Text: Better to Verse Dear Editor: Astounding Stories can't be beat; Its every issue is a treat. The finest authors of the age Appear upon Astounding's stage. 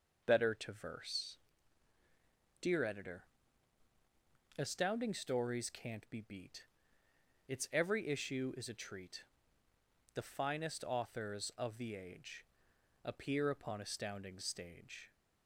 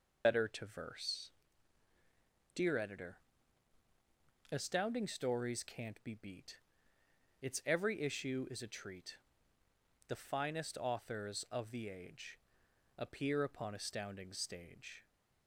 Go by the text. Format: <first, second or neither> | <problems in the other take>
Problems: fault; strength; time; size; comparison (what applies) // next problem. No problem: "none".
first | loses the start of "Better"; at 0.2 s; 70 ms // pauses between "Verse" and "Dear"; at 1.2 s; 1.2 s long; also in the first // pauses between "age" and "Appear"; noticeable; at 12.3 s; 0.60 s long; noticeable in the first